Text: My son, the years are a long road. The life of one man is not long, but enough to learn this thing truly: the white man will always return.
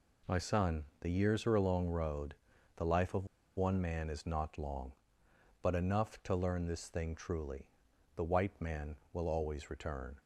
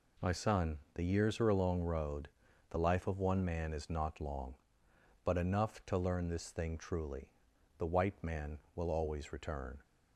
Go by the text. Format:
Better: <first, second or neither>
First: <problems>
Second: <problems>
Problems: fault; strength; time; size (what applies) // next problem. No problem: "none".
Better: second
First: pauses between "of" and "one"; slight; at 3.2 s; 0.30 s long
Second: none